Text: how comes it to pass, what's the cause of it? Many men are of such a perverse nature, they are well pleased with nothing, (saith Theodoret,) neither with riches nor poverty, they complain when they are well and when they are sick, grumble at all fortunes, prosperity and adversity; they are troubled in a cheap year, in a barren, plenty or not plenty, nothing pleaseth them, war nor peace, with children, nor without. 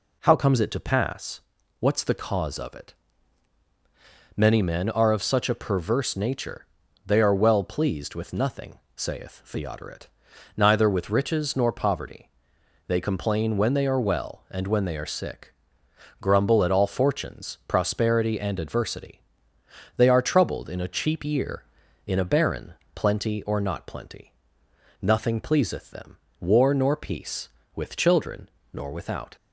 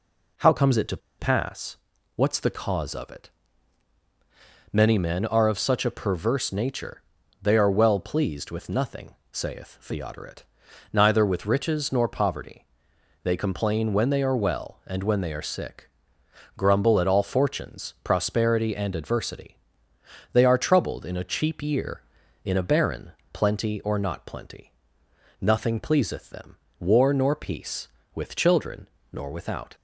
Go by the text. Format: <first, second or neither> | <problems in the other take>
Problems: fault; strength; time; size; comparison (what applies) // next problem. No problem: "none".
first | pauses between "to" and "pass"; slight; at 0.9 s; 0.21 s long